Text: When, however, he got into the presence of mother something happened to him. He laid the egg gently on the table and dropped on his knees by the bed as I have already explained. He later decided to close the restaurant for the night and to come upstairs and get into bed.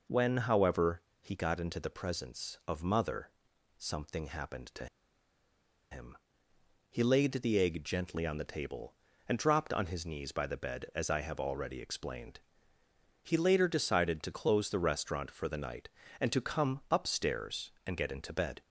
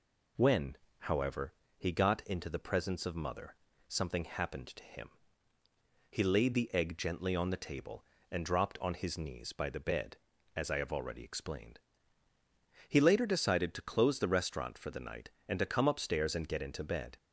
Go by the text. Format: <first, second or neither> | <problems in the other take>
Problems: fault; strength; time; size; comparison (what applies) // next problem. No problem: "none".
second | pauses between "mother" and "something"; noticeable; at 3.3 s; 0.48 s long; slight in the second // pauses between "to" and "him"; at 4.8 s; 1.0 s long